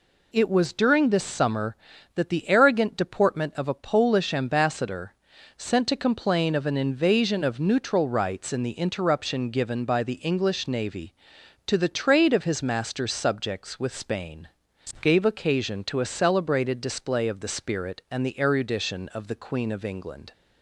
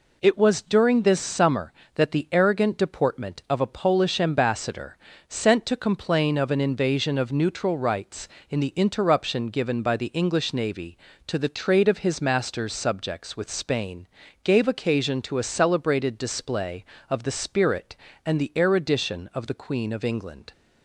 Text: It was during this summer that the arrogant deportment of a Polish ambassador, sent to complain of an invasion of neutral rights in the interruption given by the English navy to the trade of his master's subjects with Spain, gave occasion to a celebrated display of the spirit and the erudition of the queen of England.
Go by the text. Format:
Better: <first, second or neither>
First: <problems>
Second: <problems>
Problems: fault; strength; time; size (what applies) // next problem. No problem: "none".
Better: neither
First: none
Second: none